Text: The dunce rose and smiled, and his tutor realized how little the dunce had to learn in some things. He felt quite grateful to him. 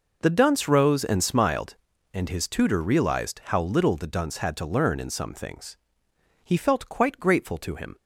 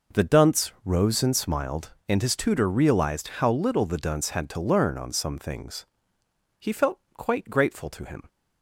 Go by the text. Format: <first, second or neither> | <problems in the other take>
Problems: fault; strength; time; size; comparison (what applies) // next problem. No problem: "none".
first | says "on" for "in"; at 4.9 s // pauses between "felt" and "quite"; slight; at 6.9 s; 0.16 s long